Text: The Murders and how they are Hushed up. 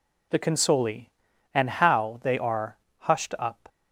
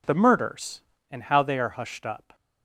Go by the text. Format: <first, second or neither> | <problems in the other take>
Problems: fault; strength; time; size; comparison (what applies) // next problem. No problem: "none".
second | says "Consoli" for "Murders"; at 0.4 s // pauses between "are" and "Hushed"; slight; at 2.7 s; 0.22 s long